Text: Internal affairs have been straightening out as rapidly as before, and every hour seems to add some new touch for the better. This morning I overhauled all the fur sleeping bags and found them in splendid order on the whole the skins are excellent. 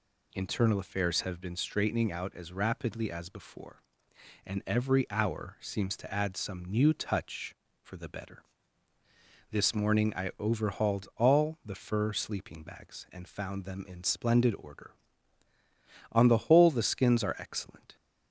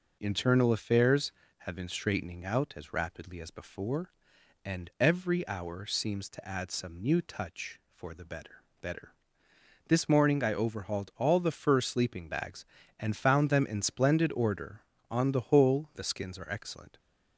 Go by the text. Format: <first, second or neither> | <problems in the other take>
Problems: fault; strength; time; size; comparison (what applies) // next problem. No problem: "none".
first | says "better" twice; at 8.8 s